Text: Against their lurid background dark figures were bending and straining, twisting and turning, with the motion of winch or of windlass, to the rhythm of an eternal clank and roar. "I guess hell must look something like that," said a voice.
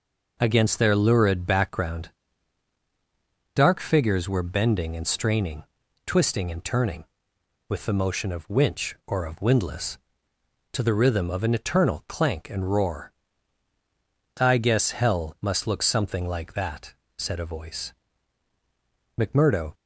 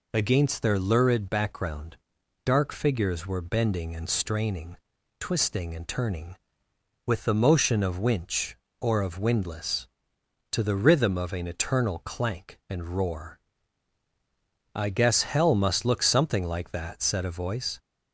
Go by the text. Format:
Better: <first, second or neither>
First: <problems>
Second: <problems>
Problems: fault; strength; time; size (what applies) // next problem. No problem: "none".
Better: second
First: pauses between "background" and "dark"; strong; at 2.0 s; 1.4 s long // goes on to say "McMurdo"; from 19.1 s on; 0.56 s long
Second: pauses between "background" and "dark"; noticeable; at 1.9 s; 0.48 s long